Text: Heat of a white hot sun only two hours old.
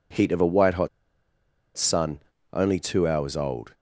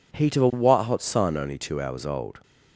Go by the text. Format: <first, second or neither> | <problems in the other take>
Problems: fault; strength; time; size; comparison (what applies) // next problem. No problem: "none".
second | pauses between "hot" and "sun"; noticeable; at 0.8 s; 0.89 s long // pauses between "sun" and "only"; slight; at 2.1 s; 0.34 s long